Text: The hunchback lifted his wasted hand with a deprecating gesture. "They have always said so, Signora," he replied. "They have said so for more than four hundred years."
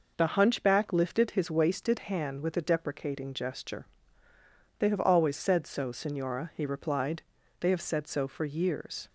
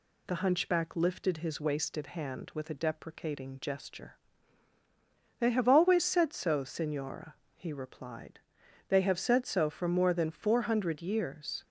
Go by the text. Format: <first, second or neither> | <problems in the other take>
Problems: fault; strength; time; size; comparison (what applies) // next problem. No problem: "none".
second | skips "more than four hundred"; at 8.4 s